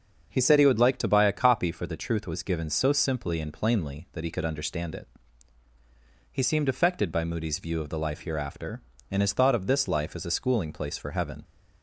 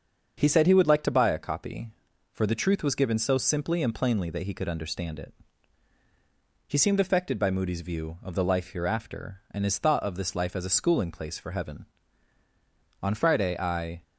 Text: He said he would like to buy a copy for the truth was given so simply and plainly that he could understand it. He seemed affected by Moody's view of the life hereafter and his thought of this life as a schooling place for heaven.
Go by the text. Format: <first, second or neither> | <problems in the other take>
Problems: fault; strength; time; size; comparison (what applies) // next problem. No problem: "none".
first | starts louder than the rest; until 1.3 s; 7 dB; also in the first // goes on to say "On Friday I"; noticeable; from 13.0 s on; 1.0 s long